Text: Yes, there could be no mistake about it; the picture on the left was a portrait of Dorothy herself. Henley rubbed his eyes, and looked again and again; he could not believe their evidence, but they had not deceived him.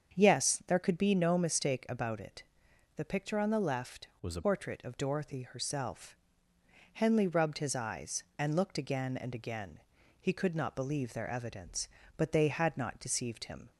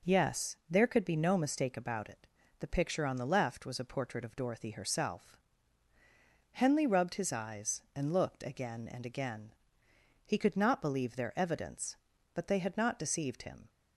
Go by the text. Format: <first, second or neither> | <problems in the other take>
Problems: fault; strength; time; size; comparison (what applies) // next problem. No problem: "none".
second | starts louder than the rest; strong; until 1.1 s; 7.5 dB // changes voice from "was" to "a"; from 4.2 to 4.4 s; 0.2 s long